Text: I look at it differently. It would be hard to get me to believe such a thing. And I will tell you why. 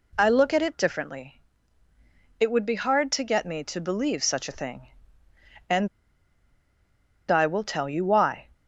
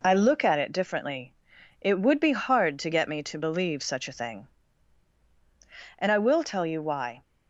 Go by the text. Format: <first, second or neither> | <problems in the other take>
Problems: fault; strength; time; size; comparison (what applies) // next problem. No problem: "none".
second | pauses between "And" and "I"; strong; at 5.8 s; 1.4 s long